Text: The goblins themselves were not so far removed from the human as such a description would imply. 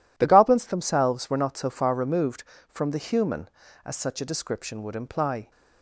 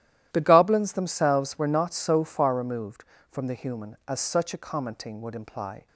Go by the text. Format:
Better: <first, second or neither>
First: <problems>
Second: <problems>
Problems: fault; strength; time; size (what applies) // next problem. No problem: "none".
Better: first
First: none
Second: starts louder than the rest; strong; until 1.3 s; 12.5 dB // says "commenting" for "description"; at 4.5 s